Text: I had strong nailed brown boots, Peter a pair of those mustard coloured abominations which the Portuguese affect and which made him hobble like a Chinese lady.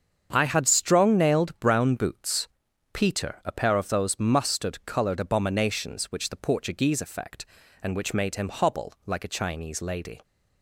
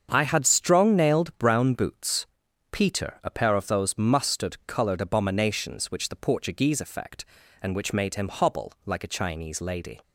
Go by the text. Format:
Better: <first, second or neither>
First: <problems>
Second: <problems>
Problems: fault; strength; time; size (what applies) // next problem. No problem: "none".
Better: neither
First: starts louder than the rest; strong; until 1.3 s; 7.5 dB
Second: starts louder than the rest; strong; until 1.1 s; 7.5 dB